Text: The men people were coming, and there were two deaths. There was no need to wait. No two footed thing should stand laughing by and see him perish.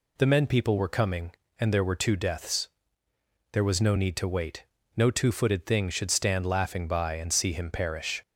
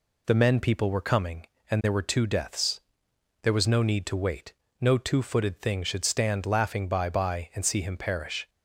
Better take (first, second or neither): first